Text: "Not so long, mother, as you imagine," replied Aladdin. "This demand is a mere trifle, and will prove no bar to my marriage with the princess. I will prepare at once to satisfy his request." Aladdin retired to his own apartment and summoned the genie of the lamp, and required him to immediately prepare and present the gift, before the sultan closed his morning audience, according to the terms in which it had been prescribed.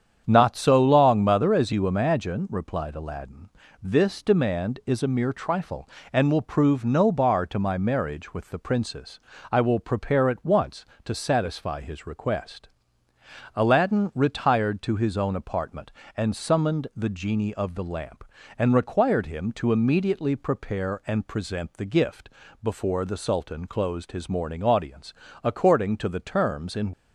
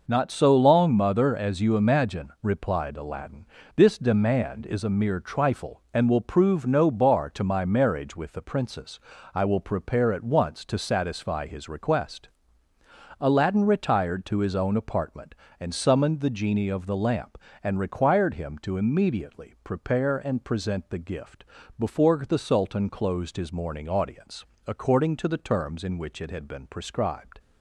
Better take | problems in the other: second | starts louder than the rest; strong; until 1.2 s; 8 dB // stops before "which it had been prescribed"; at 26.9 s

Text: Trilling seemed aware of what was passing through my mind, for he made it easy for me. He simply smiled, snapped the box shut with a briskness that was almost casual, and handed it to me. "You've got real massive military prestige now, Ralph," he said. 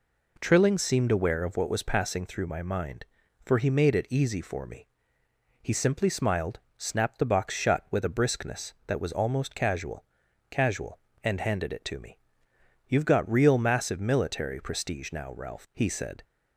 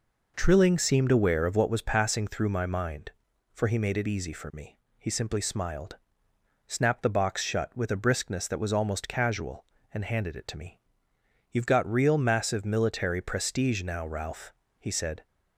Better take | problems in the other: second | says "casual" twice; at 10.5 s

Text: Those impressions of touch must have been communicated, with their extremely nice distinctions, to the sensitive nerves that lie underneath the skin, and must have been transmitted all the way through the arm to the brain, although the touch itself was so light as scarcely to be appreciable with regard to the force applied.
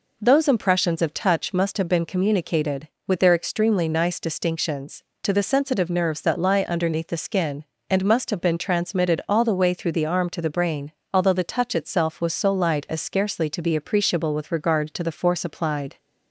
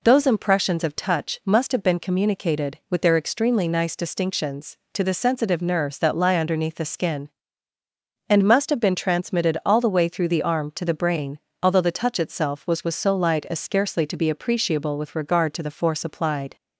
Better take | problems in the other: first | says "was" twice; at 12.8 s

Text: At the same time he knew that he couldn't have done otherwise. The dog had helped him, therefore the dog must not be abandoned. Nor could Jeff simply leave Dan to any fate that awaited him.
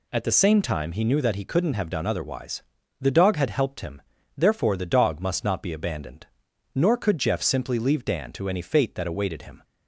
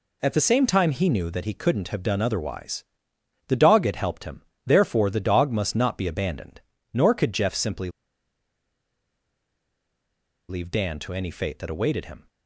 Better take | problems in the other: first | pauses between "simply" and "leave"; strong; at 7.8 s; 2.6 s long

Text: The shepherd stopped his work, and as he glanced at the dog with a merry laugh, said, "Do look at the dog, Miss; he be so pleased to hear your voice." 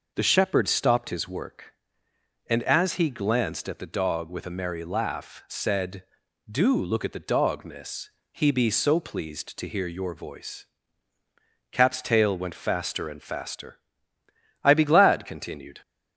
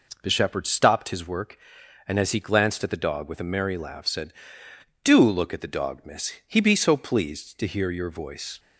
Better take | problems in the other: second | goes on to say "Cap's tail went faster and faster I be glad continued"; strong; from 11.7 s on; 4.0 s long

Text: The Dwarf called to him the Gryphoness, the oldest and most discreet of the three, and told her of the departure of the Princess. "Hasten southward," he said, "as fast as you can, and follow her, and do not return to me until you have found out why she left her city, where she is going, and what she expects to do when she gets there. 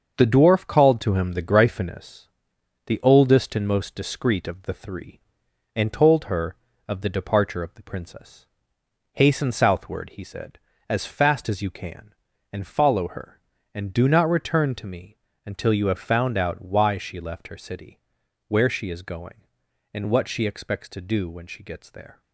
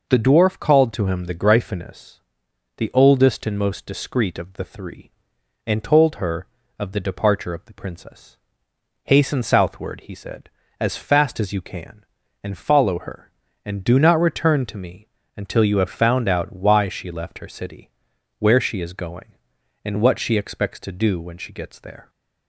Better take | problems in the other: second | gets quieter; throughout; 6.5 dB // pauses between "me" and "until"; slight; at 15.1 s; 0.26 s long; slight in the second

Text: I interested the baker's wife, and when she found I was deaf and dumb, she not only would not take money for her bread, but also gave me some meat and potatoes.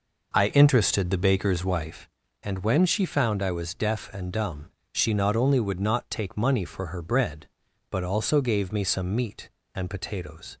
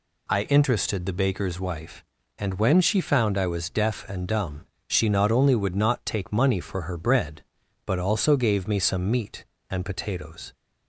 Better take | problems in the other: second | starts louder than the rest; noticeable; until 2.0 s; 5 dB

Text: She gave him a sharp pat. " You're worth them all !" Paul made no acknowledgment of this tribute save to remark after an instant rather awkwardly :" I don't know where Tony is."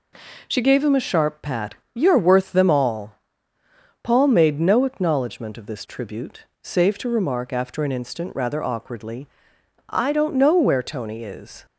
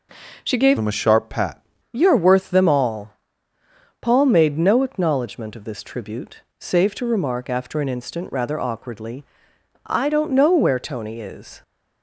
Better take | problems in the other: first | changes voice from "him" to "pat"; from 0.7 to 1.6 s; 0.9 s long // pauses between "tribute" and "save"; slight; at 6.4 s; 0.16 s long; slight in the first

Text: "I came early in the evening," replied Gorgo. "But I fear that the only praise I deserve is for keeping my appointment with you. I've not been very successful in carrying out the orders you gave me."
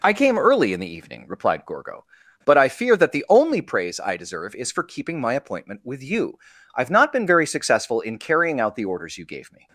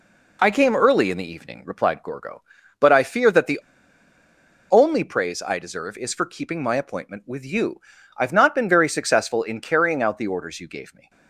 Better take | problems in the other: first | pauses between "the" and "only"; at 3.6 s; 1.0 s long

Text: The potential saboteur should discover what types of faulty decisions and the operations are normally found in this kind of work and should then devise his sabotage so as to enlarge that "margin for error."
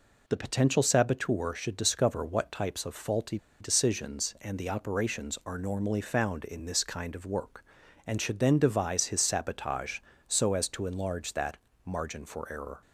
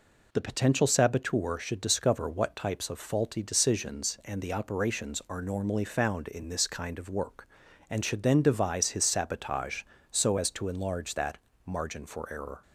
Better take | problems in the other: second | pauses between "faulty" and "decisions"; slight; at 3.3 s; 0.22 s long // pauses between "that" and "margin"; slight; at 11.5 s; 0.28 s long; slight in the second

